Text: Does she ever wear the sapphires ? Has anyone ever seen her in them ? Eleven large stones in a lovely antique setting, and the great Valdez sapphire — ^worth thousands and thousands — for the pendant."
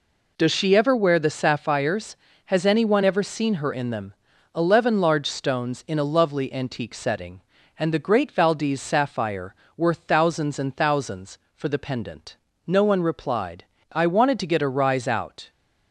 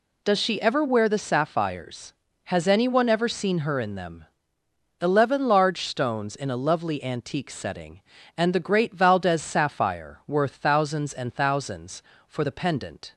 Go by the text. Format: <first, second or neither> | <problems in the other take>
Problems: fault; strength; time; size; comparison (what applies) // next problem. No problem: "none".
second | goes on to say "No one replied I wanted to get a rise out"; strong; from 12.6 s on; 2.8 s long